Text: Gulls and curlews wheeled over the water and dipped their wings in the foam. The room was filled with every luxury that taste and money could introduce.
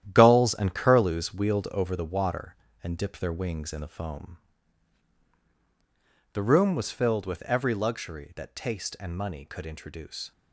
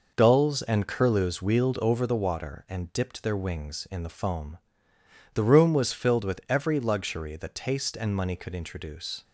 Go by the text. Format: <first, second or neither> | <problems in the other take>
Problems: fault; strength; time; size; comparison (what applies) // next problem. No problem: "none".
second | gets quieter; strong; throughout; 9.5 dB